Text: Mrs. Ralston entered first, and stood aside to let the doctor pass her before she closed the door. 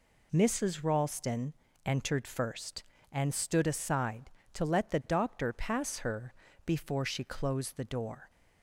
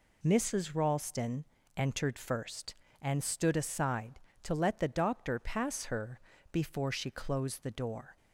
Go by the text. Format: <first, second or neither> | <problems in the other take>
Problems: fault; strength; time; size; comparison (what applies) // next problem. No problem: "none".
neither | pauses between "Ralston" and "entered"; slight; the same in both // pauses between "her" and "before"; slight; the same in both